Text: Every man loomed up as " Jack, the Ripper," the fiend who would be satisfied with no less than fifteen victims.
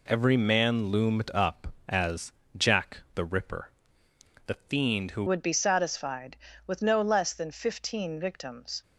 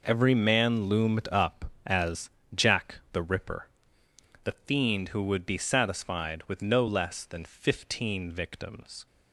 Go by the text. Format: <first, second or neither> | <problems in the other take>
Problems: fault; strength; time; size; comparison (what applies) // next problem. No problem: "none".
second | changes voice at "would"; from 5.2 s on; 3.6 s long